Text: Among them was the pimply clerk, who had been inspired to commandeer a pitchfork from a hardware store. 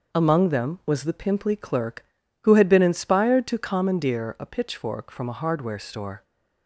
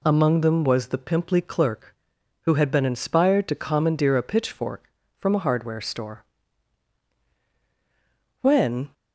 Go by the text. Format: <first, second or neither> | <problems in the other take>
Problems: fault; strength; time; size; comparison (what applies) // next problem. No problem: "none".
first | goes on to say "When"; from 8.4 s on; 0.52 s long